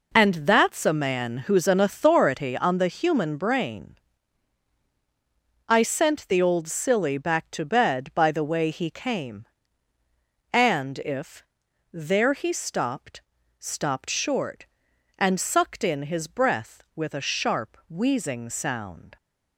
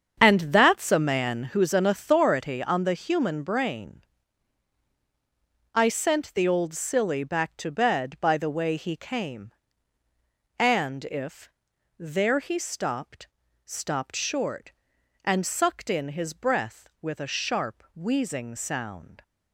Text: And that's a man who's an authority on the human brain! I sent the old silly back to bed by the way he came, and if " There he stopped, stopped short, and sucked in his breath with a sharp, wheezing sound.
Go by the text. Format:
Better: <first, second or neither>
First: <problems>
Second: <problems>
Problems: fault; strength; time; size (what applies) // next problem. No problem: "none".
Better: first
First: none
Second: starts louder than the rest; strong; until 1.5 s; 7.5 dB